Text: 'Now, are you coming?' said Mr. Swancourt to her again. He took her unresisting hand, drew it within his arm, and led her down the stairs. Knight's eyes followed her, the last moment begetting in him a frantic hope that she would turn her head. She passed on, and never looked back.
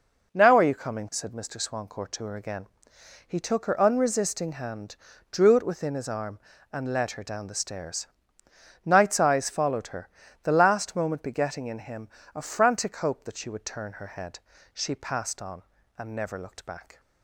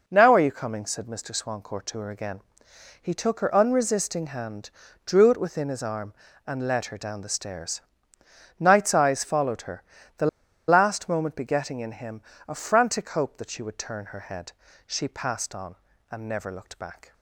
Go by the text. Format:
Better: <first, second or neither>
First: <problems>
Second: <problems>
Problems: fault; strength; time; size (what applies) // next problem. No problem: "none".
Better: first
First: pauses between "him" and "a"; slight; at 12.0 s; 0.26 s long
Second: pauses between "the" and "last"; at 10.2 s; 0.41 s long // pauses between "him" and "a"; slight; at 12.2 s; 0.26 s long